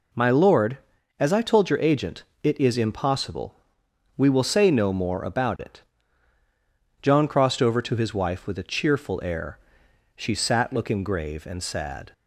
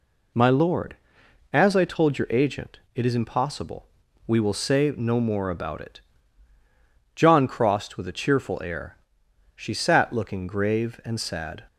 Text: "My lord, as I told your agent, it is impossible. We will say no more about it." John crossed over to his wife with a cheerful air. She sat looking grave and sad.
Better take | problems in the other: first | skips "over to his wife"; at 7.9 s

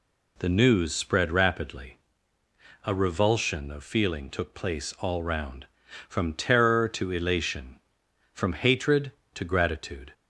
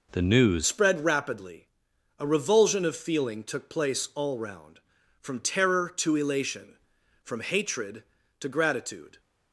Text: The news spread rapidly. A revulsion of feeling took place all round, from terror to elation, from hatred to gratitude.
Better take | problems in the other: first | changes voice at "spread"; from 0.6 s on; 8.5 s long

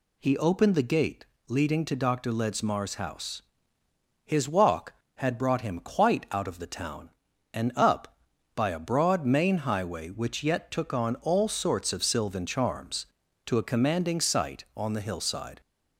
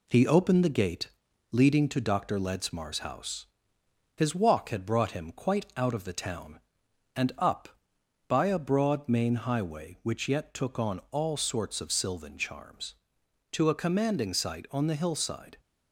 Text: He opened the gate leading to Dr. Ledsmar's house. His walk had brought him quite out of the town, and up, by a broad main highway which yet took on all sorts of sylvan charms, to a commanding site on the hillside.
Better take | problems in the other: first | gets quieter; slight; throughout; 3 dB // pauses between "gate" and "leading"; at 1.0 s; 0.42 s long; slight in the first

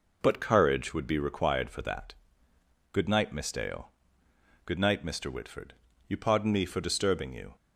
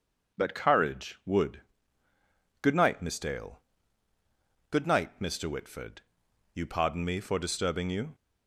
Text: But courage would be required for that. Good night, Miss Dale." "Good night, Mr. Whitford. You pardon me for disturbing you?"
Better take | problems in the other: first | skips "be required for that"; at 2.1 s

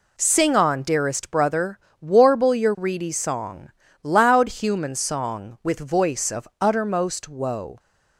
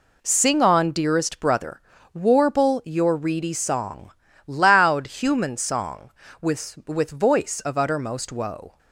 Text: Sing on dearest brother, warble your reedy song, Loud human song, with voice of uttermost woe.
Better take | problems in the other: first | says "with" twice; at 6.8 s

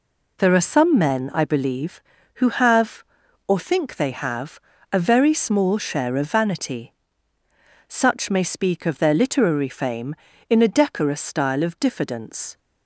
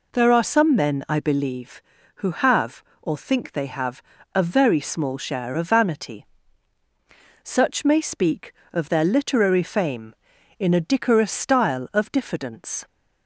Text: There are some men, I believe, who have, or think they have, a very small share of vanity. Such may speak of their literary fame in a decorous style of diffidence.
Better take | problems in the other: neither | none

